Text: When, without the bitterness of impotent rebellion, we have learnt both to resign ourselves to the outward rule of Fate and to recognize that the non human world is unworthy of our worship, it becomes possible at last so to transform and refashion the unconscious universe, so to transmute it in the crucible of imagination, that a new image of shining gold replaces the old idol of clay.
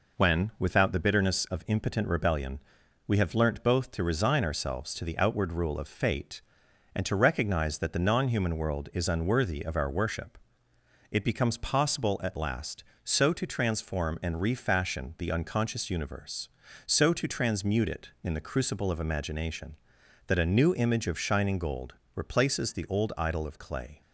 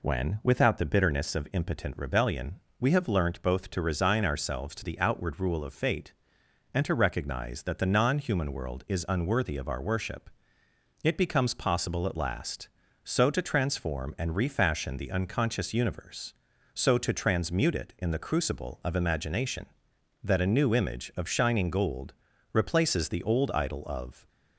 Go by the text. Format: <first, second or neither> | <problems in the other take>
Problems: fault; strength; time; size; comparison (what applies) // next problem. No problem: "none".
first | pauses between "gold" and "replaces"; at 22.1 s; 0.38 s long; slight in the first // stops before "clay"; at 24.2 s